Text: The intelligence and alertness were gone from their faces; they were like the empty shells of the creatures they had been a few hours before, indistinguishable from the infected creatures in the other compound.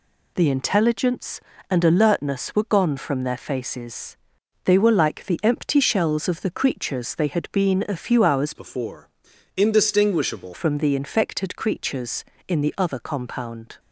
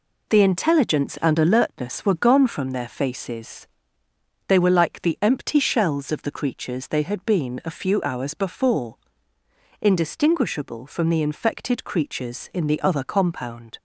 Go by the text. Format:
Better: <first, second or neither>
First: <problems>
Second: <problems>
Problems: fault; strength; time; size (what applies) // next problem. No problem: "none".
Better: second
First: changes voice from "before" to "indistinguishable"; from 8.5 to 10.5 s; 2.0 s long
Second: none